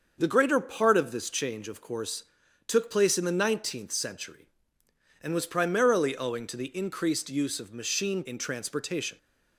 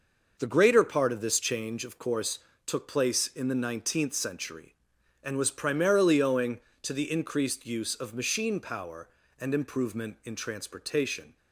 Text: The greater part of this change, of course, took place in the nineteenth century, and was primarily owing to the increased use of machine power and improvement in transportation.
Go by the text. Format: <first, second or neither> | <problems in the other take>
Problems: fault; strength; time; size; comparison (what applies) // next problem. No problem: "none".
second | starts louder than the rest; until 1.1 s; 6.5 dB // skips "power and improvement"; at 8.2 s